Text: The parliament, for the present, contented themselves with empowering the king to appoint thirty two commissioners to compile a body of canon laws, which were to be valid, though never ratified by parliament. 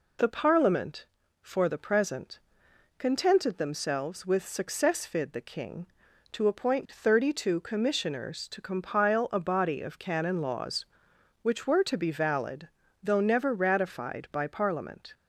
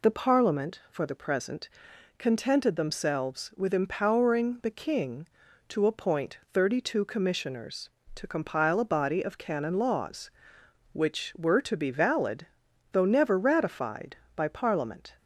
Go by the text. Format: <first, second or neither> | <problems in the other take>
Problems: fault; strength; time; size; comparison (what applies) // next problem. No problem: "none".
second | says "successfid" for "empowering"; at 4.4 s